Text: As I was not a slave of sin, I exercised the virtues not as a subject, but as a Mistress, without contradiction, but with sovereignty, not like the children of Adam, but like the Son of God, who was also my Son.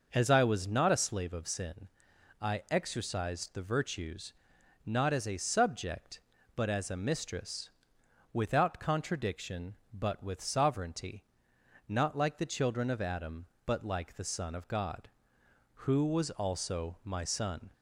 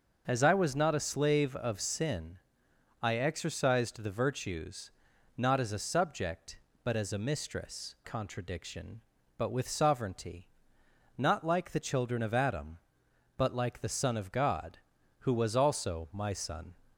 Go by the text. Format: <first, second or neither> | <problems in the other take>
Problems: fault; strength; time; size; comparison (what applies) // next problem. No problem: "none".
first | pauses between "virtues" and "not"; noticeable; at 4.9 s; 0.46 s long; noticeable in the first // skips "without"; at 7.9 s